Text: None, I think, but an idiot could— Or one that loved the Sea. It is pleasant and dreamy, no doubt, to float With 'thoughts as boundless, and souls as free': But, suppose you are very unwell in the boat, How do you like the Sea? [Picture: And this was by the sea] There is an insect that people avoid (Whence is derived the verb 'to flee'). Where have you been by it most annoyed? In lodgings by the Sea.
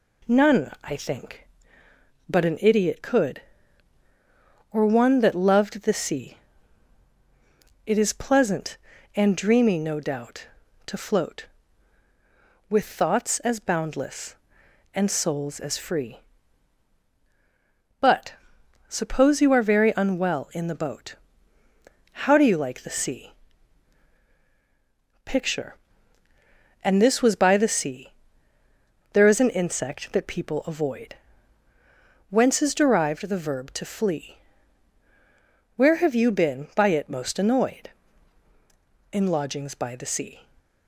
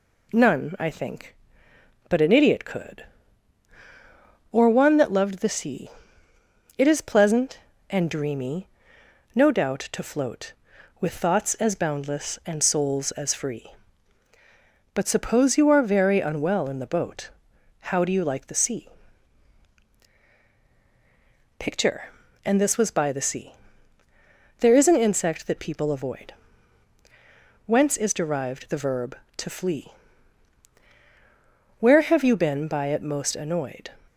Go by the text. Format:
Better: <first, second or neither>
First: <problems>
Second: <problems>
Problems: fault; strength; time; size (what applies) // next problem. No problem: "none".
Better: first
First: pauses between "sea" and "There"; noticeable; at 28.1 s; 0.98 s long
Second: pauses between "sea" and "There"; at 23.5 s; 1.0 s long // stops before "In lodgings by the Sea"; at 34.0 s